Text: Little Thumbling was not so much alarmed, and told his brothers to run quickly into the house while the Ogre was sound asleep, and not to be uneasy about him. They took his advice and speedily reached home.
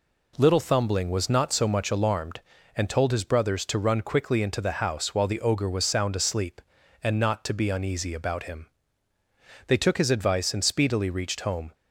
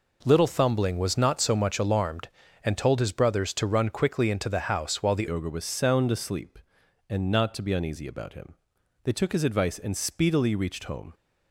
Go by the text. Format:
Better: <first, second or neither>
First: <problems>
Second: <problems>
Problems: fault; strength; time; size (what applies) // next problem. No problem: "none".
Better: first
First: none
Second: changes voice at "Ogre"; from 5.2 s on; 5.9 s long